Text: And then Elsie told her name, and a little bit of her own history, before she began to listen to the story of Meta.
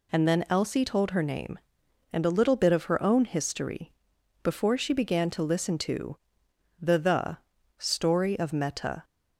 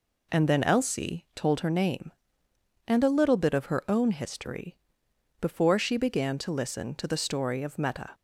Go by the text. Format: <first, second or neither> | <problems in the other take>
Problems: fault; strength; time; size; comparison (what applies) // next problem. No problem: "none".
second | pauses between "to" and "the"; noticeable; at 6.1 s; 0.64 s long // says "the" twice; at 6.9 s